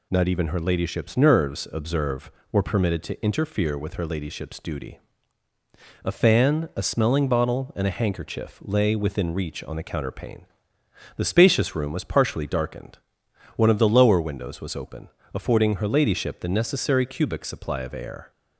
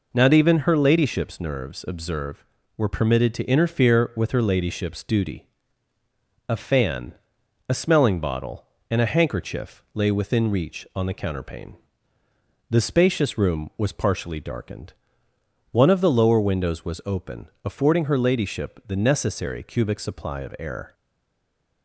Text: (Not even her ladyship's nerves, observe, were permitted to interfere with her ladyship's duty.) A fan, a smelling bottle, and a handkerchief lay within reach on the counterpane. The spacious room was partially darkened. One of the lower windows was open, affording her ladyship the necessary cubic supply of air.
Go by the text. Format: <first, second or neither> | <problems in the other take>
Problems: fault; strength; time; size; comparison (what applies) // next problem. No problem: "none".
first | stays silent after the last word; slight; from 20.9 s on; 0.9 s long